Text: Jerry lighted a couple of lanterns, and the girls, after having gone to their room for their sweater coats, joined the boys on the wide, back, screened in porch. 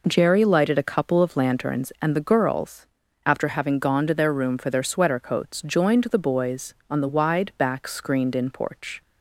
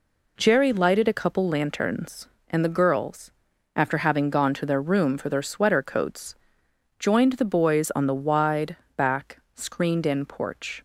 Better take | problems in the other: first | skips "of"; at 1.4 s

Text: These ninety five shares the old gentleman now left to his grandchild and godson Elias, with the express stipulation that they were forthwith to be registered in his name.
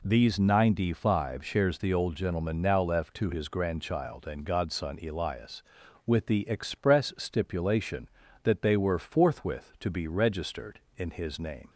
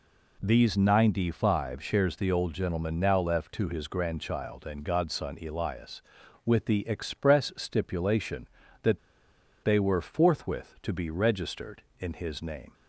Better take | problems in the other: first | pauses between "that" and "they"; noticeable; at 8.9 s; 0.65 s long

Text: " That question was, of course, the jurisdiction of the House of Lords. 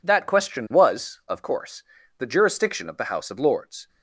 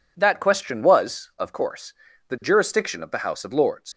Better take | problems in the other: first | leaves "Lords" unfinished; at 3.9 s; 95 ms

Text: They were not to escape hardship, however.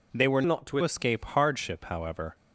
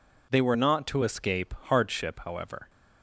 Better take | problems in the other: second | changes voice from "not" to "to"; from 0.4 to 0.7 s; 0.3 s long

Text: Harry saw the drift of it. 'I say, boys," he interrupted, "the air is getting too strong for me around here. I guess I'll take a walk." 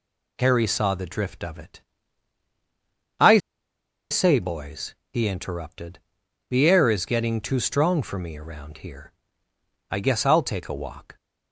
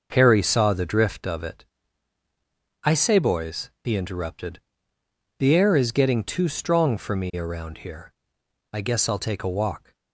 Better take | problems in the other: second | pauses between "I" and "say"; noticeable; at 3.3 s; 0.73 s long

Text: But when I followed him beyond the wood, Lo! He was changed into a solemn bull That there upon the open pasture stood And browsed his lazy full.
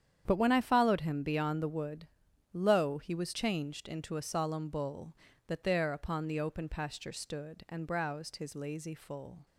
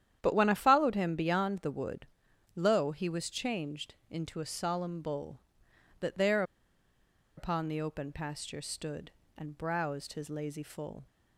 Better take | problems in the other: first | starts louder than the rest; strong; until 1.2 s; 10 dB; strong in the first // pauses between "changed" and "into"; slight; at 3.9 s; 0.16 s long // pauses between "there" and "upon"; noticeable; at 6.4 s; 0.94 s long

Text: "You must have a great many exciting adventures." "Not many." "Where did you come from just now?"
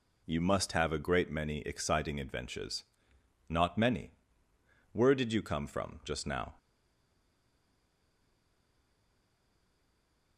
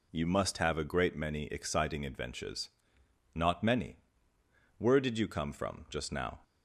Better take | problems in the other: second | stays silent after the last word; strong; from 6.5 s on; 3.8 s long

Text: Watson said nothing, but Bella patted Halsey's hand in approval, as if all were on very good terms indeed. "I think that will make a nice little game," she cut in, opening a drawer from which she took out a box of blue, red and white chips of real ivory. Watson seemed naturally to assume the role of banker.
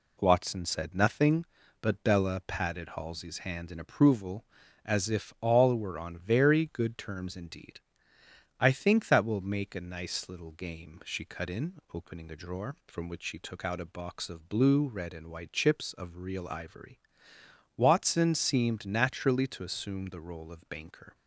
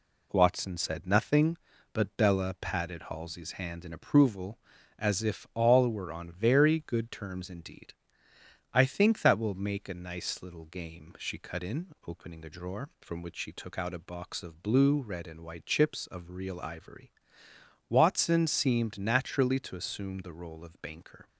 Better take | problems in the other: neither | none

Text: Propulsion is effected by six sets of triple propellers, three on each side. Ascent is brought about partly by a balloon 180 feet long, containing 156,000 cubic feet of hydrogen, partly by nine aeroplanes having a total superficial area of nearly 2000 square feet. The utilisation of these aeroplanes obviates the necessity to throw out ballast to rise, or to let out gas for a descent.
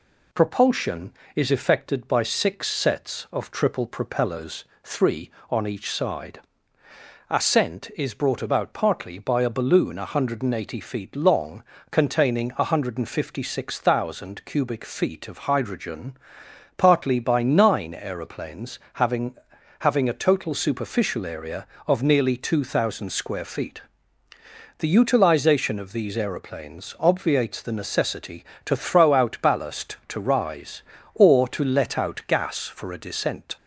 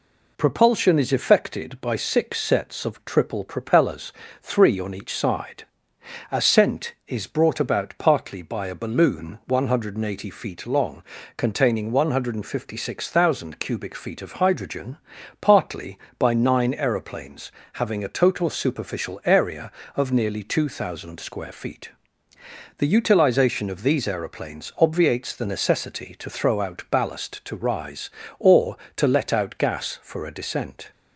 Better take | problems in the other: second | pauses between "aeroplanes" and "having"; slight; at 18.7 s; 0.16 s long; slight in the second // says "having" twice; at 19.7 s

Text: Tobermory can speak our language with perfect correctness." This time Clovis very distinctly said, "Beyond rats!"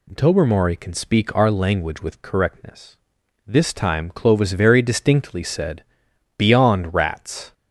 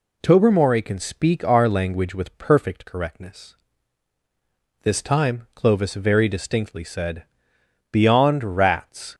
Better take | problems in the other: second | skips "perfect"; at 2.2 s

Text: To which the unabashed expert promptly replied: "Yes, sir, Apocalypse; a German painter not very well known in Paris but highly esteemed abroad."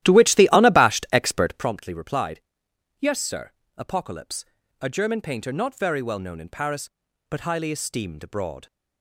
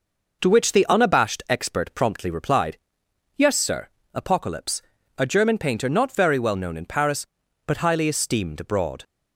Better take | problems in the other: second | starts louder than the rest; strong; until 1.7 s; 13.5 dB

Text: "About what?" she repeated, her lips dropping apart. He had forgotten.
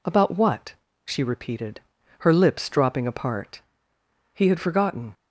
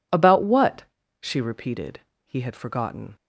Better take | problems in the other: first | skips "her lips dropping apart"; at 2.1 s

